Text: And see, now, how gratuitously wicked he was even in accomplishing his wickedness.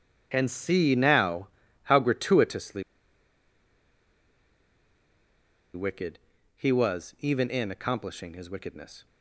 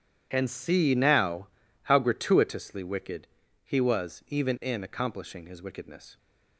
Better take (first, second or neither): second